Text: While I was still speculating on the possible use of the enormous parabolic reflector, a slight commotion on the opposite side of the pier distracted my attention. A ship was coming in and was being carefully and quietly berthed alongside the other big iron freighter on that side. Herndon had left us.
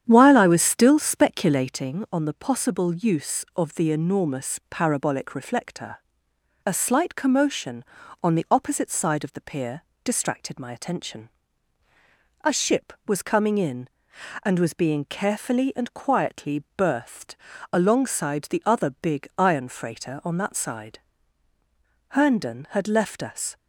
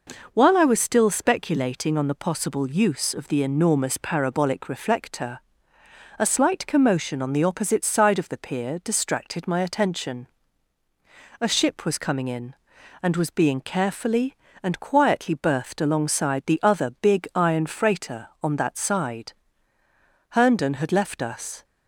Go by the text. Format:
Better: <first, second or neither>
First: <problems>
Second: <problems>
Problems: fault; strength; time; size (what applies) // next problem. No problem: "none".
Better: second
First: starts louder than the rest; strong; until 1.9 s; 9 dB // pauses between "pier" and "distracted"; slight; at 9.8 s; 0.22 s long // pauses between "berthed" and "alongside"; at 17.3 s; 0.38 s long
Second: none